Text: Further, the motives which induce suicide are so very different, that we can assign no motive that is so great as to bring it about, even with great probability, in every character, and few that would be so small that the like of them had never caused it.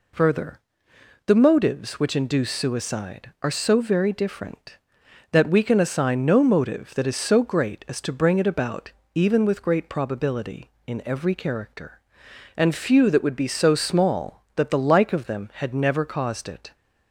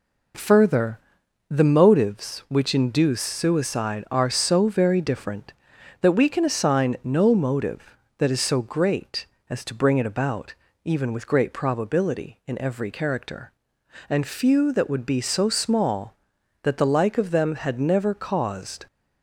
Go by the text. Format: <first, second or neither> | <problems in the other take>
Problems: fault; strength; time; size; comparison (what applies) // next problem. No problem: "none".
first | stops before "it"; at 18.8 s